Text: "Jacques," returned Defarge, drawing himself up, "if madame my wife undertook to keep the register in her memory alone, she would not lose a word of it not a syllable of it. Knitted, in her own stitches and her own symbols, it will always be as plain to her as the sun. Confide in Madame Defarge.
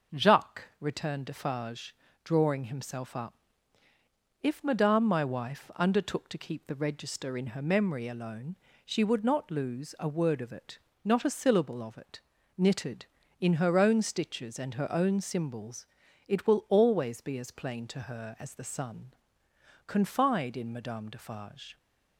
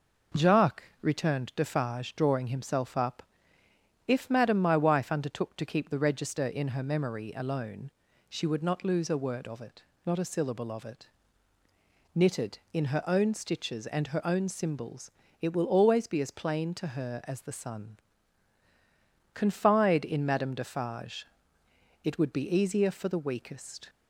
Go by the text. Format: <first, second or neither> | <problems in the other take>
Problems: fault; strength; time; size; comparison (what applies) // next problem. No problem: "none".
first | pauses between "it" and "not"; slight; at 9.8 s; 0.24 s long; slight in the first // goes on to say "It would be easier for the weakest"; strong; from 22.0 s on; 1.8 s long